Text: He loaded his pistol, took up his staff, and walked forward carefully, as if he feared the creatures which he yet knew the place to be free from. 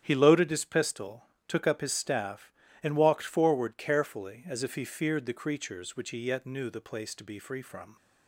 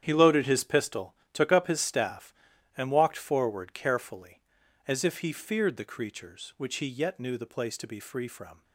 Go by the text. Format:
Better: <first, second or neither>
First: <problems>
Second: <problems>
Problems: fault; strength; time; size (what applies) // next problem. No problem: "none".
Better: neither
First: starts louder than the rest; strong; until 1.0 s; 9.5 dB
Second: starts louder than the rest; strong; until 1.0 s; 9.5 dB